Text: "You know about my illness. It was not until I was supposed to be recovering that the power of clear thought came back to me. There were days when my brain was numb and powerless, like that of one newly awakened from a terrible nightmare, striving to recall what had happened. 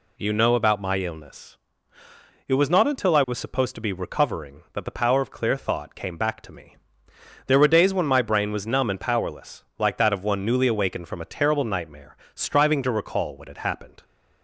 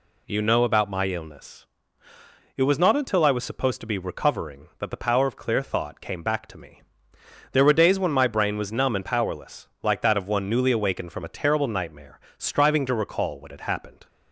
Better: neither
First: none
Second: none

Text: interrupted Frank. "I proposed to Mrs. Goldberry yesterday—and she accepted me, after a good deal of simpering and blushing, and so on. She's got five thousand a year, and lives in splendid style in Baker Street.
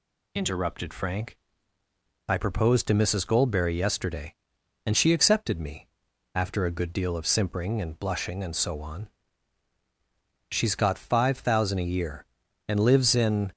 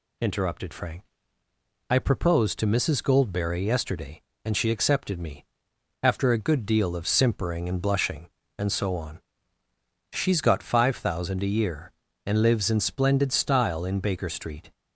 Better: second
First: stops before "splendid style in Baker Street"; at 13.5 s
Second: none

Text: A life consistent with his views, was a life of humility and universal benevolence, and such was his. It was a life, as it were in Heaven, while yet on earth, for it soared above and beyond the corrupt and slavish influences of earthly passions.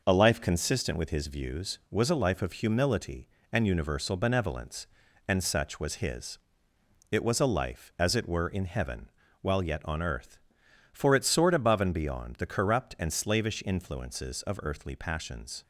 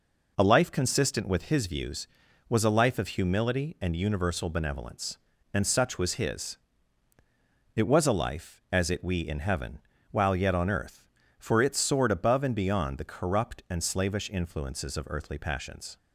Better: first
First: none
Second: says "we" for "were"; at 9.0 s

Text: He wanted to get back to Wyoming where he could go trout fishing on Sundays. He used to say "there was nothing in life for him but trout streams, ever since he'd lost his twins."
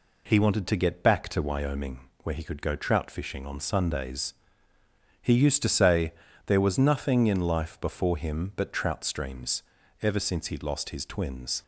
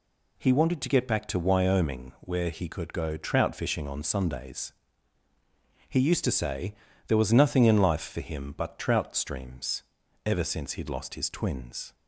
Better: second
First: pauses between "Wyoming" and "where"; slight; at 2.0 s; 0.24 s long // pauses between "say" and "there"; slight; at 6.1 s; 0.34 s long // says "before" for "for"; at 7.7 s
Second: pauses between "say" and "there"; slight; at 6.7 s; 0.34 s long

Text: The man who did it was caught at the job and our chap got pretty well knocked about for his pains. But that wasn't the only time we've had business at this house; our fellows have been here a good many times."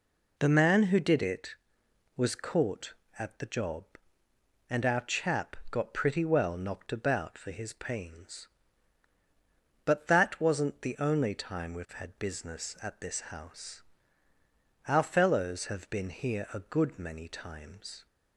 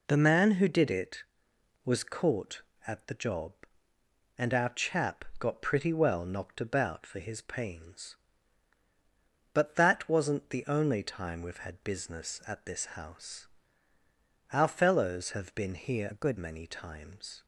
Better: first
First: none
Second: changes voice from "a" to "good"; from 16.1 to 16.3 s; 0.2 s long

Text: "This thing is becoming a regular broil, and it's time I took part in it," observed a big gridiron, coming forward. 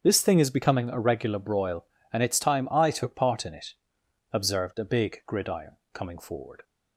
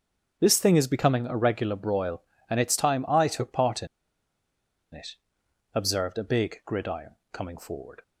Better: first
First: starts louder than the rest; strong; until 1.0 s; 7.5 dB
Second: starts louder than the rest; strong; until 1.4 s; 7.5 dB // pauses between "in" and "it"; at 3.8 s; 1.0 s long

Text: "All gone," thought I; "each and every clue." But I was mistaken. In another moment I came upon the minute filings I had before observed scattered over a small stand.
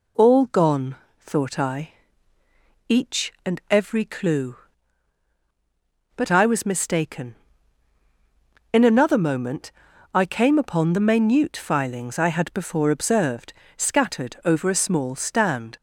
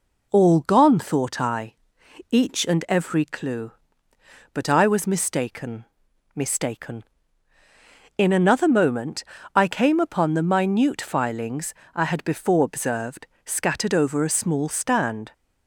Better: first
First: pauses between "moment" and "I"; at 9.7 s; 0.42 s long // pauses between "observed" and "scattered"; slight; at 13.5 s; 0.24 s long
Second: says "mistaken" twice; at 6.3 s // pauses between "moment" and "I"; slight; at 9.2 s; 0.32 s long // pauses between "filings" and "I"; slight; at 11.7 s; 0.22 s long // pauses between "observed" and "scattered"; slight; at 13.2 s; 0.22 s long

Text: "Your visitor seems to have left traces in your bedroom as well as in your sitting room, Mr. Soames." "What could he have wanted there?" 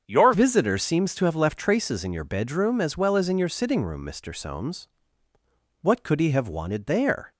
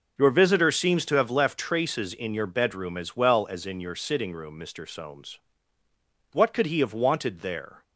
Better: second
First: starts louder than the rest; strong; until 1.0 s; 7 dB // changes voice at "visitor"; from 0.3 s on; 7.0 s long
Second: none

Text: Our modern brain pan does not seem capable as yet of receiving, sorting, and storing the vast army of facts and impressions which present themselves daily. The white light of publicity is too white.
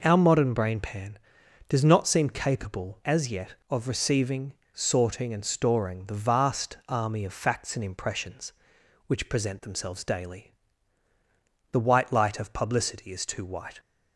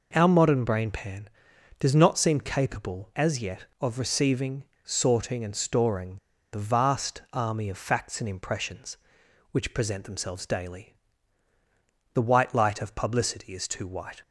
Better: first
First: none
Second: pauses between "storing" and "the"; at 6.1 s; 0.36 s long

